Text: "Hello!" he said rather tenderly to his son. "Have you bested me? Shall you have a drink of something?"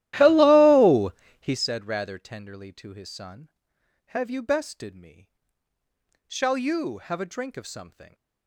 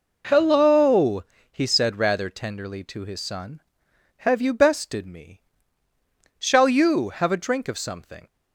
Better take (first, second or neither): second